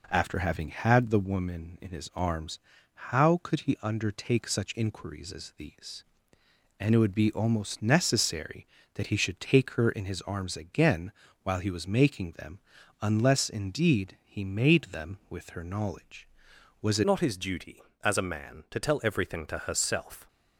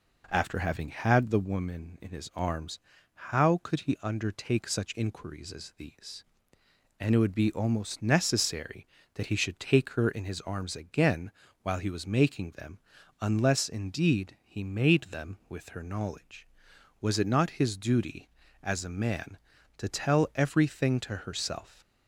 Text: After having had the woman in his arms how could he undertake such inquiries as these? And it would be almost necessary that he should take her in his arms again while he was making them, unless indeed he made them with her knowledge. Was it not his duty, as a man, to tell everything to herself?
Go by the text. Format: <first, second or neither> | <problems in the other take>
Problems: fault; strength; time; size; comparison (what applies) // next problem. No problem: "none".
second | pauses between "arms" and "how"; noticeable; at 2.5 s; 0.50 s long; noticeable in the second // pauses between "again" and "while"; slight; at 11.1 s; 0.32 s long; slight in the second // changes voice at "not"; from 17.0 s on; 3.2 s long